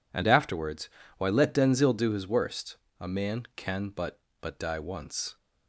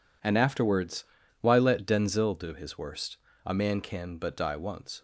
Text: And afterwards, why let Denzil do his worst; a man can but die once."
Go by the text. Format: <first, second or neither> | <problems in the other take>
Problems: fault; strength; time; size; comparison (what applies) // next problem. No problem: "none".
second | says "but" twice; at 4.4 s